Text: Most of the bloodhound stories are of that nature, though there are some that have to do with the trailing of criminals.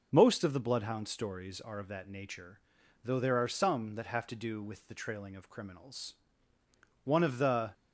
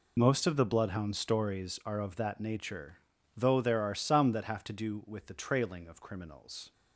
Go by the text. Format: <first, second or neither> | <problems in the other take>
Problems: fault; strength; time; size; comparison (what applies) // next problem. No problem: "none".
second | goes on to say "One of the"; noticeable; from 7.0 s on; 0.68 s long